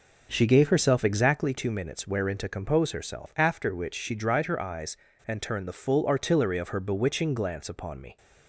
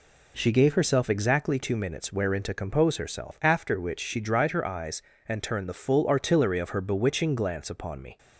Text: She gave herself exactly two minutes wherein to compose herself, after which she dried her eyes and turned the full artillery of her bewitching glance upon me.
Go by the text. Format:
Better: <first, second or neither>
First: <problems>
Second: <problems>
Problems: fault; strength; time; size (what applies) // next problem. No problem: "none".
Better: second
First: starts louder than the rest; noticeable; until 1.5 s; 5.5 dB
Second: none